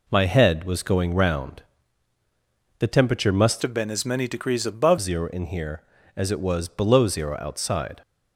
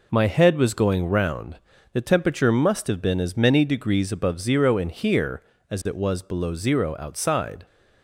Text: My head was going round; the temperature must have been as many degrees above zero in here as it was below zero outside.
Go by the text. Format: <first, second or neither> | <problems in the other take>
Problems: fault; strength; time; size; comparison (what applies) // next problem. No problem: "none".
second | changes voice from "have" to "above"; from 3.6 to 4.9 s; 1.3 s long